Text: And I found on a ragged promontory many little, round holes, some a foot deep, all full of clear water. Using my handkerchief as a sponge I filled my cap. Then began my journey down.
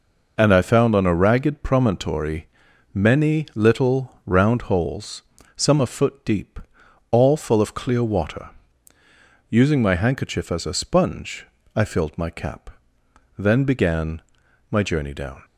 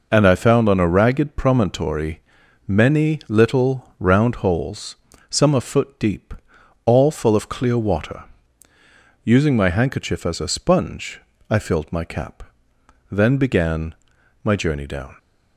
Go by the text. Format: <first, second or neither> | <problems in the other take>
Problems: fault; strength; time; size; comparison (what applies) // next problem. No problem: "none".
neither | pauses between "promontory" and "many"; noticeable; the same in both // pauses between "sponge" and "I"; slight; the same in both // pauses between "began" and "my"; noticeable; the same in both